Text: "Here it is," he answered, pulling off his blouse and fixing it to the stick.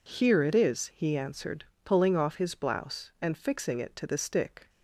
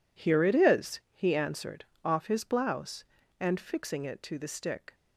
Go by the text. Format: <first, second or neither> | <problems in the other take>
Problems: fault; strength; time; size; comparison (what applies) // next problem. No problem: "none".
first | skips "pulling"; at 1.9 s